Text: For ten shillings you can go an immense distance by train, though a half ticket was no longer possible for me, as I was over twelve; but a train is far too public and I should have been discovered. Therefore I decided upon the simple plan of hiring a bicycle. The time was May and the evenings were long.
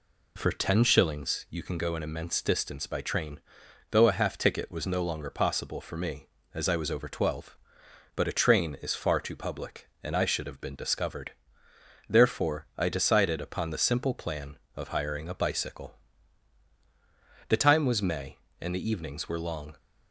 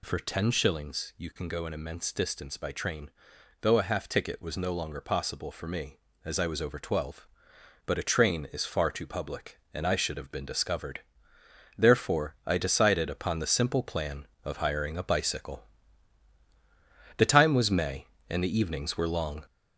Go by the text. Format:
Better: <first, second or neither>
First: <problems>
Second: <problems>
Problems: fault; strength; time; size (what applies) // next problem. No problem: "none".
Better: first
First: none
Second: gets louder; noticeable; throughout; 5.5 dB